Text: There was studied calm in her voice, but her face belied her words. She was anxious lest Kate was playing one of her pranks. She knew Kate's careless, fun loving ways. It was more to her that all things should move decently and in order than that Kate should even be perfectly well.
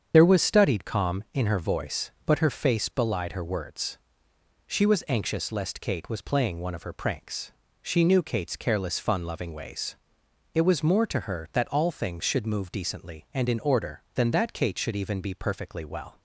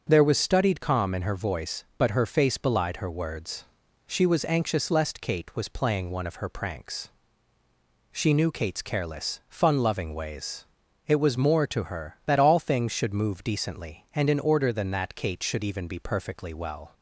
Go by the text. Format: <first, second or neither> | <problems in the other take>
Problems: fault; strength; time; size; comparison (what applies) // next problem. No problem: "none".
second | loses the start of "There"; at 0.1 s; 50 ms // starts louder than the rest; strong; until 1.1 s; 7.5 dB; also in the second